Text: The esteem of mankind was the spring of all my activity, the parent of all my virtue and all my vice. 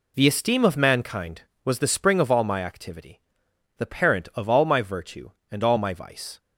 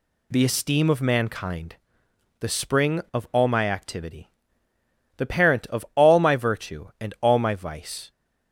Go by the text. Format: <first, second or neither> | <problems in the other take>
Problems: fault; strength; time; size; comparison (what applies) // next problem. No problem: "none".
first | skips "was"; at 2.0 s